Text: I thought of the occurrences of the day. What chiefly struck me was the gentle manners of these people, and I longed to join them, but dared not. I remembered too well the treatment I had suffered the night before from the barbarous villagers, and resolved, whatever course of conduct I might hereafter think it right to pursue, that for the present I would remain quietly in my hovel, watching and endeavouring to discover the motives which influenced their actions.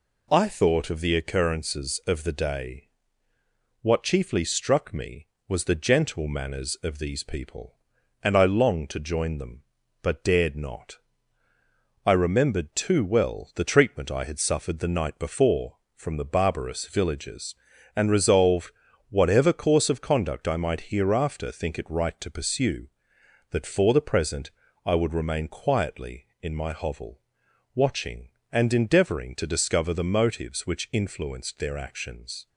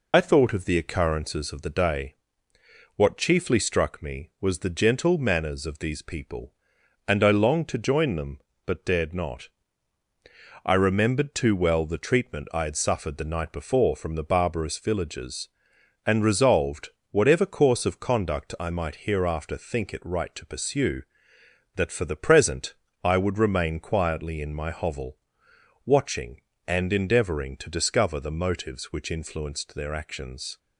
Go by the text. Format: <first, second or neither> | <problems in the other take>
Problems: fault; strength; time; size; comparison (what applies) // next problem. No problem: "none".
first | loses the start of "I"; at 0.1 s; 40 ms // pauses between "present" and "I"; slight; at 22.7 s; 0.28 s long; slight in the first